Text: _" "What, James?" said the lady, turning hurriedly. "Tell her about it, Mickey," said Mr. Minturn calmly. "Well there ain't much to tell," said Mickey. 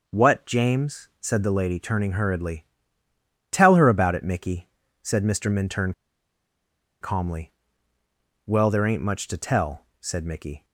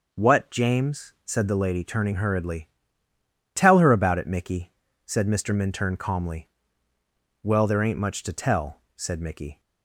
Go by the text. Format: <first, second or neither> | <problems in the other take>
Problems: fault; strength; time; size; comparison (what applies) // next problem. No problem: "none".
second | pauses between "Minturn" and "calmly"; at 5.9 s; 1.0 s long